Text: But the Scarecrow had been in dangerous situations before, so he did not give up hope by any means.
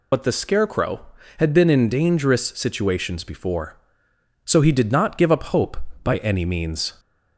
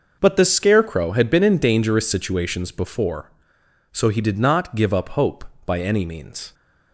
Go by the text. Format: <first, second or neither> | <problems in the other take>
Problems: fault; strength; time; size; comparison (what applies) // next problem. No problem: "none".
second | loses the start of "But"; at 0.1 s; 80 ms